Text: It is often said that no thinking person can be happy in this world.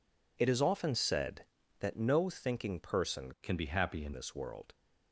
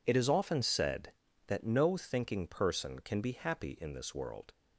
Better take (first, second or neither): second